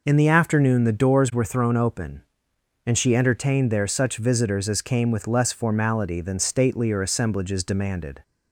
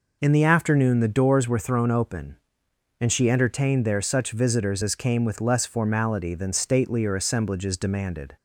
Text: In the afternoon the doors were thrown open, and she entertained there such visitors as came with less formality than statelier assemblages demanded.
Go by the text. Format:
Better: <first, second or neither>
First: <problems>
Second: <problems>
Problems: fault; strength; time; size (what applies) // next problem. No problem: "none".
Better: neither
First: none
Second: none